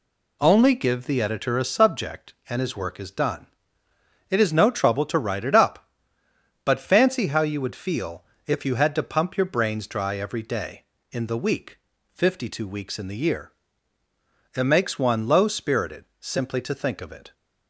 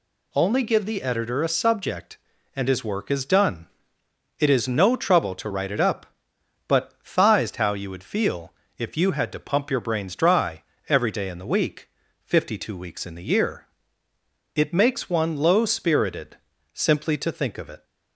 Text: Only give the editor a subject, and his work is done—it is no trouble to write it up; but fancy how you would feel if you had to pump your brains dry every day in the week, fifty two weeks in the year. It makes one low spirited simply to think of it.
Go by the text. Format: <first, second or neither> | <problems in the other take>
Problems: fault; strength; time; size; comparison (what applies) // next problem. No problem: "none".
first | says "thized" for "fancy"; at 7.0 s // pauses between "feel" and "if"; slight; at 8.5 s; 0.24 s long; slight in the first // pauses between "dry" and "every"; slight; at 10.6 s; 0.26 s long // pauses between "spirited" and "simply"; slight; at 16.3 s; 0.36 s long